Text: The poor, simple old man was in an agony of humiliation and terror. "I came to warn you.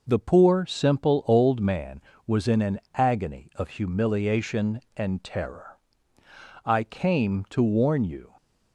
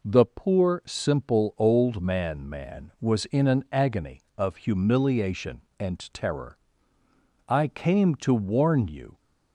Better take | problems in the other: first | says "man" twice; at 2.4 s // pauses between "and" and "terror"; slight; at 5.9 s; 0.16 s long

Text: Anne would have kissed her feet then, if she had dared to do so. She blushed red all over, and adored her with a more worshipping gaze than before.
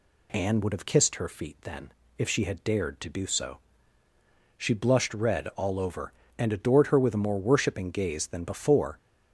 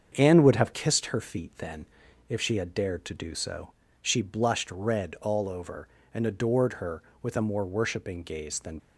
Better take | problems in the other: first | starts louder than the rest; strong; until 1.1 s; 7 dB // stops before "before"; at 8.7 s

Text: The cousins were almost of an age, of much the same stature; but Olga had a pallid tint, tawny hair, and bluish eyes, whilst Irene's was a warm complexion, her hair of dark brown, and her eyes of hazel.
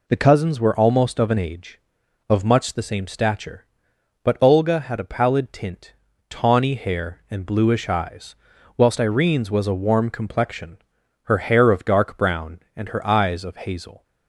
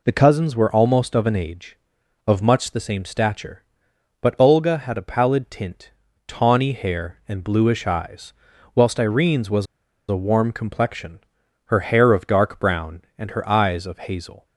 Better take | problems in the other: first | pauses between "was" and "a"; at 9.6 s; 0.45 s long

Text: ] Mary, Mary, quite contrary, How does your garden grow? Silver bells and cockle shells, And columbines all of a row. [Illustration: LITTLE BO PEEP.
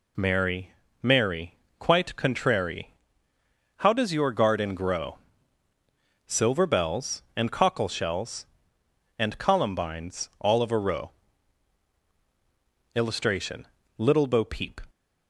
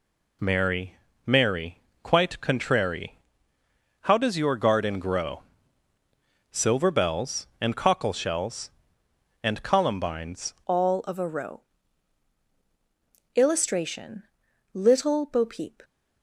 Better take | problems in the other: first | changes voice at "all"; from 10.6 s on; 5.2 s long

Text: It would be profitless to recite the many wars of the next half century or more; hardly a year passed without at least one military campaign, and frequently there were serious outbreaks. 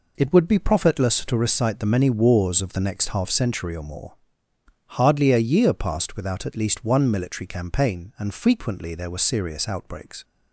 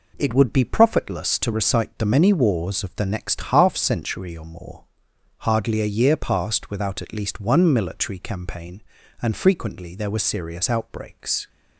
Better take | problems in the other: neither | none

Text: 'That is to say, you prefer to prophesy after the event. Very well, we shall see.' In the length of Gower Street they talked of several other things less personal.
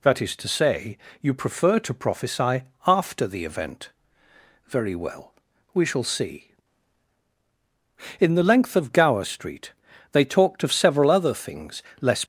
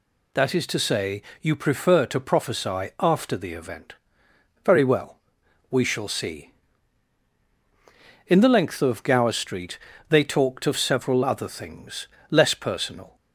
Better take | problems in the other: second | pauses between "prophesy" and "after"; slight; at 2.6 s; 0.22 s long // pauses between "Street" and "they"; at 9.7 s; 0.38 s long; slight in the second // pauses between "things" and "less"; slight; at 11.8 s; 0.18 s long; slight in the second // stops before "personal"; at 12.2 s

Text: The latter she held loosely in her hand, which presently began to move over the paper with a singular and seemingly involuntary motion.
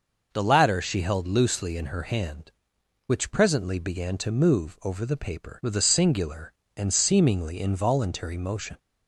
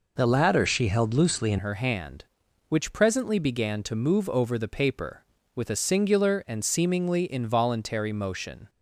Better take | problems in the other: first | changes voice at "her"; from 1.5 s on; 7.1 s long

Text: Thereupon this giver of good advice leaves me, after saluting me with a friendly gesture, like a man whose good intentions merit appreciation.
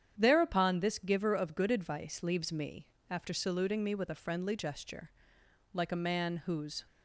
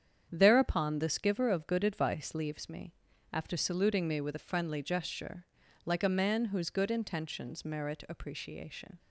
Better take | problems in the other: second | starts louder than the rest; strong; until 1.1 s; 9 dB; strong in the second // stops before "good intentions merit appreciation"; at 6.8 s

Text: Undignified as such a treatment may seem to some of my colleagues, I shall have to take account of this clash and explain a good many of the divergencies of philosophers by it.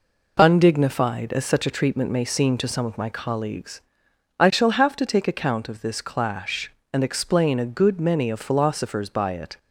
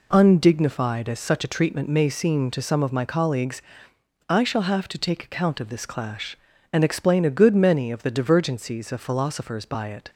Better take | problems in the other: second | skips "of the divergencies"; at 8.2 s

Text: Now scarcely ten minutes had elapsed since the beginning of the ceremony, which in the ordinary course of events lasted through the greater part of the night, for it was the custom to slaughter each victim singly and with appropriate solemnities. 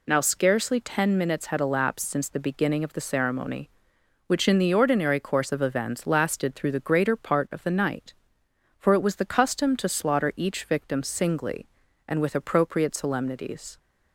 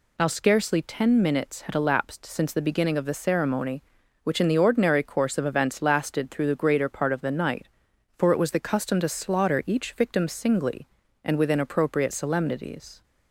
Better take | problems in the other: first | says "within" for "with"; at 11.3 s

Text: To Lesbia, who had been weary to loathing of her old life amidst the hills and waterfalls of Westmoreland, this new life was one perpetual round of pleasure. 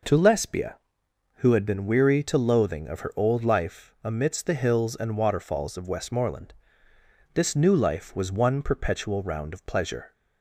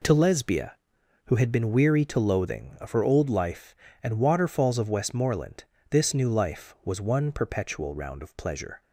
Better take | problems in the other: first | skips "amidst the hills"; at 3.8 s

